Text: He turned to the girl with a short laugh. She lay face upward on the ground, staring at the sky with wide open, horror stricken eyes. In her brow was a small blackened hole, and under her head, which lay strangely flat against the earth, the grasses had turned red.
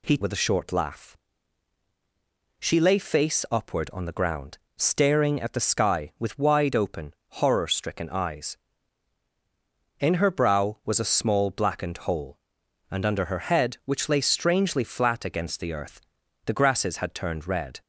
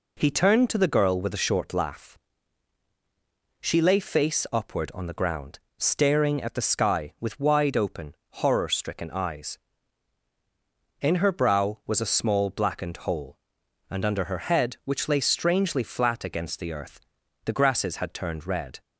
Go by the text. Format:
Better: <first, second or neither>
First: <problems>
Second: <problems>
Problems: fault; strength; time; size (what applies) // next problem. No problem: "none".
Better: second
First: skips "turned to the girl"; at 0.1 s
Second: none